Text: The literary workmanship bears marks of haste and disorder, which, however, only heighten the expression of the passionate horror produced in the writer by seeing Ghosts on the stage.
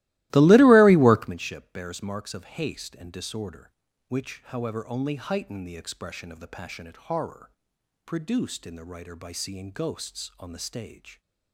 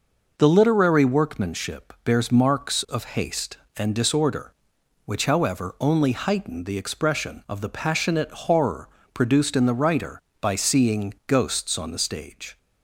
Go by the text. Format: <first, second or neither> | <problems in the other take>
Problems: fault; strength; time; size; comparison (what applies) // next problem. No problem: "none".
second | starts louder than the rest; strong; until 1.4 s; 18 dB // pauses between "horror" and "produced"; noticeable; at 7.5 s; 0.54 s long; slight in the second